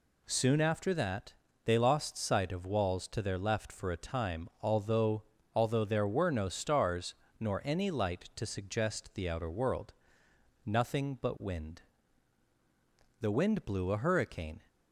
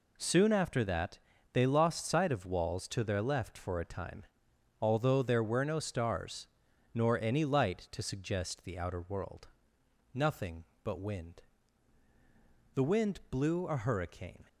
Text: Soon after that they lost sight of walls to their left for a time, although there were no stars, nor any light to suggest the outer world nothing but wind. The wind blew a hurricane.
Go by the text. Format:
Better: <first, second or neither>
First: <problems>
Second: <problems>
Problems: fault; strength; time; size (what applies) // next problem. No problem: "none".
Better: second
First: pauses between "that" and "they"; slight; at 1.3 s; 0.30 s long // says "although" twice; at 5.5 s // pauses between "world" and "nothing"; noticeable; at 9.9 s; 0.72 s long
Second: pauses between "that" and "they"; slight; at 1.1 s; 0.34 s long // pauses between "world" and "nothing"; noticeable; at 9.4 s; 0.68 s long